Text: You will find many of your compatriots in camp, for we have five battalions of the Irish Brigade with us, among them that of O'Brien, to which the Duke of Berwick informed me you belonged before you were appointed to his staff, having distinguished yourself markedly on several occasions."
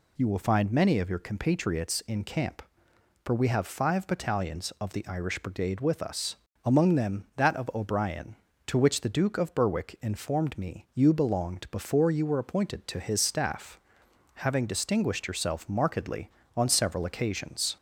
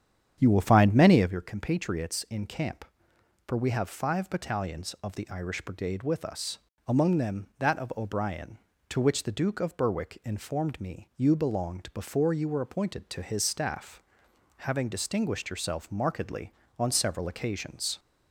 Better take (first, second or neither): first